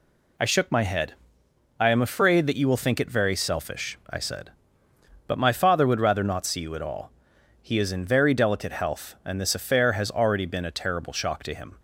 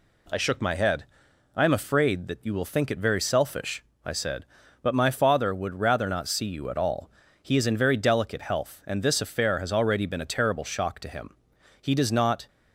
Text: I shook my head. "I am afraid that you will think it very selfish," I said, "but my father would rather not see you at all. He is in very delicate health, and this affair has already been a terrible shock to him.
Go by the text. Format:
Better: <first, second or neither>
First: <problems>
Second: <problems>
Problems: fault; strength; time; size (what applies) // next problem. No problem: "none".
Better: first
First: none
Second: goes on to say "He does not"; noticeable; from 11.8 s on; 0.66 s long